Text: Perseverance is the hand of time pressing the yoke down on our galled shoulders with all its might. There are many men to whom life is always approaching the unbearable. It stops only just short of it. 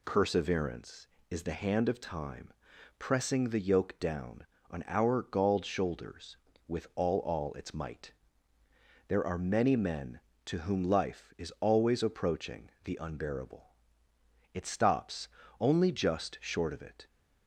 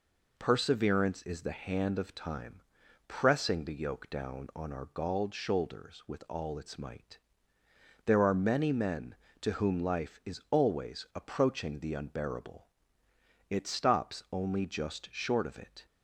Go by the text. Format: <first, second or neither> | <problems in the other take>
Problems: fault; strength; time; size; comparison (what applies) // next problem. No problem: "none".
second | pauses between "time" and "pressing"; noticeable; at 2.5 s; 0.46 s long; noticeable in the second // says "all" twice; at 7.2 s // pauses between "stops" and "only"; slight; at 15.2 s; 0.31 s long